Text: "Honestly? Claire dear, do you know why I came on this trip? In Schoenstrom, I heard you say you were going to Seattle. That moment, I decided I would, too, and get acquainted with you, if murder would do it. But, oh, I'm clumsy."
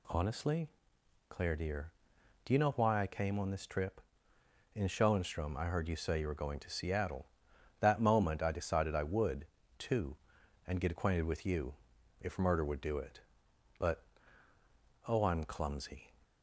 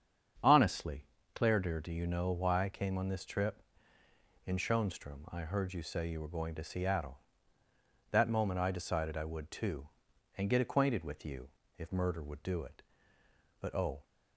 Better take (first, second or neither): first